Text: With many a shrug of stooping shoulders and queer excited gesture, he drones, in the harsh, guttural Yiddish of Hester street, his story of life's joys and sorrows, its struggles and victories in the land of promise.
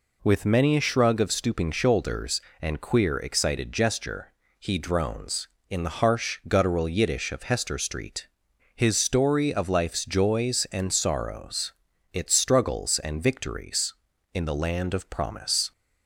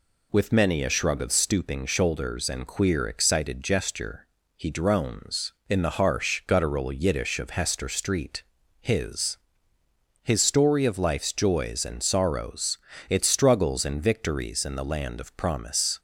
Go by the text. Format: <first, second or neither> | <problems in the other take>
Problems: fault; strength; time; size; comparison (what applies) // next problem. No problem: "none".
first | says "his" twice; at 10.2 s